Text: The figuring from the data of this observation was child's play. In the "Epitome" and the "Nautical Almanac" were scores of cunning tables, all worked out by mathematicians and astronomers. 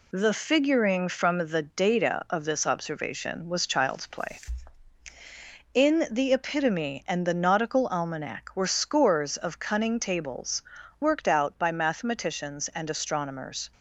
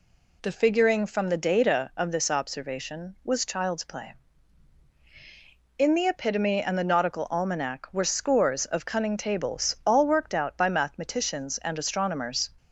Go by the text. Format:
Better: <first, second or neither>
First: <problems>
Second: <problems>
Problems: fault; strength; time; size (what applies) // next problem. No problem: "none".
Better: second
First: skips "all"; at 10.8 s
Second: none